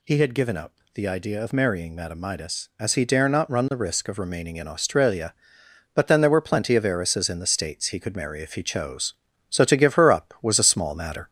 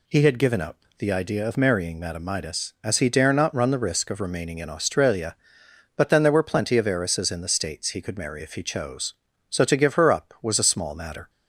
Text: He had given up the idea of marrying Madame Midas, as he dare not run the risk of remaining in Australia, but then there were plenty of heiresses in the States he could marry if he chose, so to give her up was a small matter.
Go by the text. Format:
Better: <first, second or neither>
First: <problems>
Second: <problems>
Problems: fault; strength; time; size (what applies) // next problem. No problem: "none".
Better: second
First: gets louder; slight; throughout; 3 dB // pauses between "up" and "the"; slight; at 0.7 s; 0.22 s long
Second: pauses between "up" and "the"; slight; at 0.7 s; 0.22 s long